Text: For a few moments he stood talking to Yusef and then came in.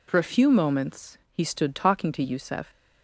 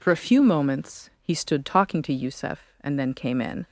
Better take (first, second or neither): second